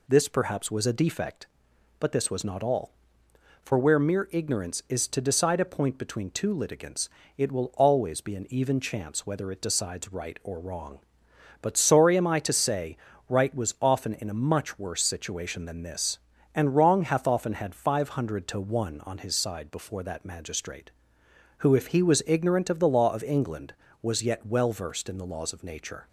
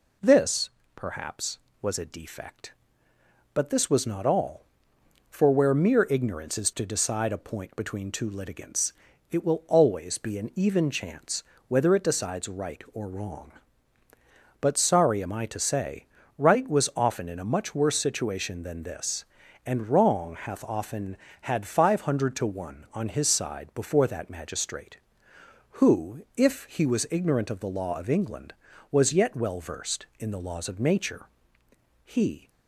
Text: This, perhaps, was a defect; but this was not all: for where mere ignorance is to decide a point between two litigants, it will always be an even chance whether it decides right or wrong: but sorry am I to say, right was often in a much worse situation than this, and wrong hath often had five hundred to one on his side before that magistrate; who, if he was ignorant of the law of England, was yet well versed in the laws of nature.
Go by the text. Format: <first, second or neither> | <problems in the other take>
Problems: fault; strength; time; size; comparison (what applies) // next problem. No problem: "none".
first | pauses between "chance" and "whether"; slight; at 11.4 s; 0.26 s long // goes on to say "He"; slight; from 32.0 s on; 0.46 s long